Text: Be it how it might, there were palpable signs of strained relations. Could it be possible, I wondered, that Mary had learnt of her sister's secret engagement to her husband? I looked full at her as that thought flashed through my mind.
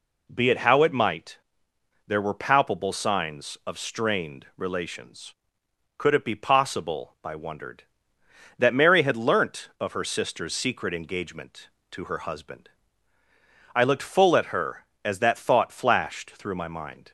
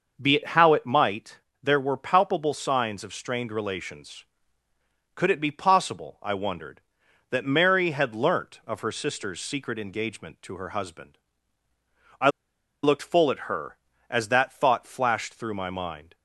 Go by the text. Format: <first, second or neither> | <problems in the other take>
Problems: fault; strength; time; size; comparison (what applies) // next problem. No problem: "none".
first | starts louder than the rest; noticeable; until 1.2 s; 6 dB // pauses between "I" and "looked"; noticeable; at 12.3 s; 0.52 s long